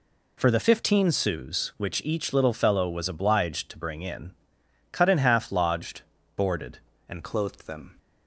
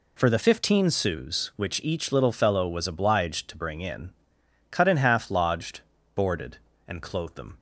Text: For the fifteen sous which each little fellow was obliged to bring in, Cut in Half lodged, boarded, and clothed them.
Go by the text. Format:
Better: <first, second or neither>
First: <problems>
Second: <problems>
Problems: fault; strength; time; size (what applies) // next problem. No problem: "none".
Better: second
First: changes voice at "clothed"; from 7.2 s on; 0.7 s long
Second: none